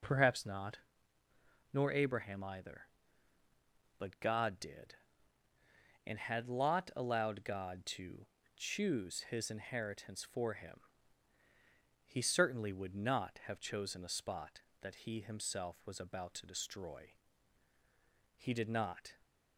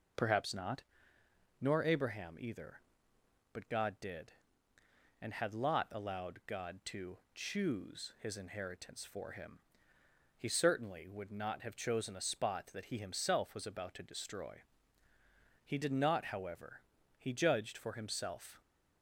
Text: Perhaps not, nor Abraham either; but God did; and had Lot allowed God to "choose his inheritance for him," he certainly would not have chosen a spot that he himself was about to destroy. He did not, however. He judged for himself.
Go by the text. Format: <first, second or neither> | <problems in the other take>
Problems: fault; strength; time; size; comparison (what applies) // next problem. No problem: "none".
second | pauses between "to" and "choose"; slight; at 8.2 s; 0.28 s long; slight in the second // stops before "however He judged for himself"; at 19.2 s